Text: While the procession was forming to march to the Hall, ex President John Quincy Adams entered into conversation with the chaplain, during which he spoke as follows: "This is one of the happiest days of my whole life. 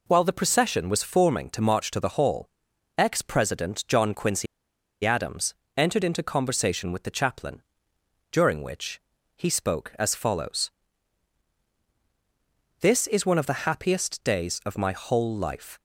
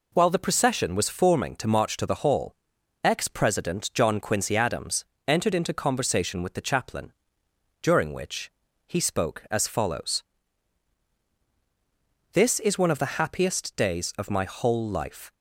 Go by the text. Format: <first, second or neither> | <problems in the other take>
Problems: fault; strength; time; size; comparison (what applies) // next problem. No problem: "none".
second | pauses between "Quincy" and "Adams"; noticeable; at 4.4 s; 0.58 s long // pauses between "Adams" and "entered"; slight; at 5.5 s; 0.22 s long; slight in the second // pauses between "which" and "he"; slight; at 9.0 s; 0.34 s long; slight in the second